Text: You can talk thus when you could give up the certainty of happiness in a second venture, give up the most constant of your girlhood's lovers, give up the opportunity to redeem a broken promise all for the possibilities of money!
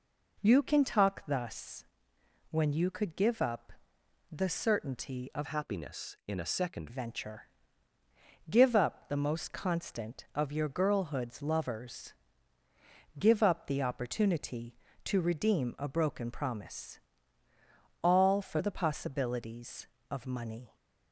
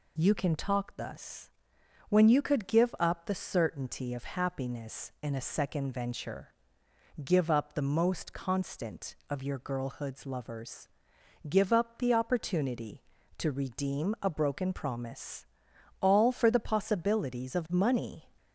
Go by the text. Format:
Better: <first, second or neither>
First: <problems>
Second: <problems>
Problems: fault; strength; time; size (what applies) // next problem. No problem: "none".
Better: second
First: pauses between "thus" and "when"; noticeable; at 1.8 s; 0.68 s long // pauses between "up" and "the"; noticeable; at 3.7 s; 0.58 s long // changes voice from "happiness" to "second"; from 5.4 to 6.8 s; 1.4 s long // pauses between "promise" and "all"; at 16.9 s; 1.0 s long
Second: pauses between "thus" and "when"; noticeable; at 1.5 s; 0.58 s long // pauses between "promise" and "all"; noticeable; at 15.4 s; 0.56 s long